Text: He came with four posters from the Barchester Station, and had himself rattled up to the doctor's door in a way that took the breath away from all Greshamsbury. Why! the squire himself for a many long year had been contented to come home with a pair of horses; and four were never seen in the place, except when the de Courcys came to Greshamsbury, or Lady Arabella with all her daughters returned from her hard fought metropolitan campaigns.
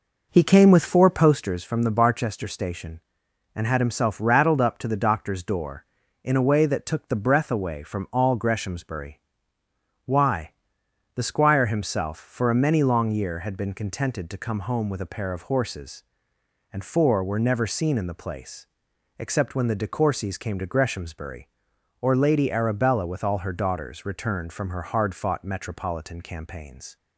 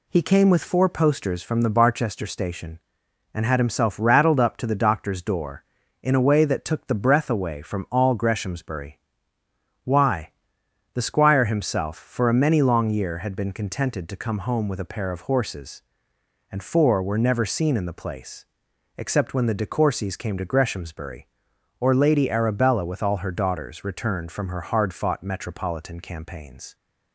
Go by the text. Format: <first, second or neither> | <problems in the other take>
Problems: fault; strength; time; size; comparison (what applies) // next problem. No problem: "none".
second | starts louder than the rest; noticeable; until 1.4 s; 5 dB